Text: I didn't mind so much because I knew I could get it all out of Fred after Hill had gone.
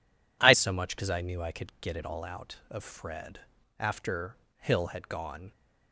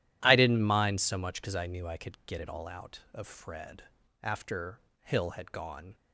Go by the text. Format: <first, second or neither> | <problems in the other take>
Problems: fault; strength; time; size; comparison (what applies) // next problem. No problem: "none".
second | skips "didn't mind"; at 0.5 s // pauses between "Fred" and "after"; at 3.4 s; 0.38 s long; also in the second // pauses between "after" and "Hill"; slight; at 4.3 s; 0.20 s long; slight in the second